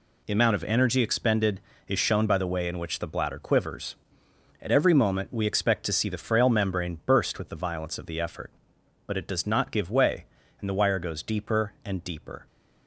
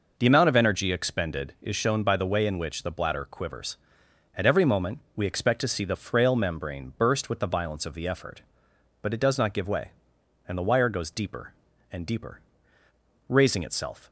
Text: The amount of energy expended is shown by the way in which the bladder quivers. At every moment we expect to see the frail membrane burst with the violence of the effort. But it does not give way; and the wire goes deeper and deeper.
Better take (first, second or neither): first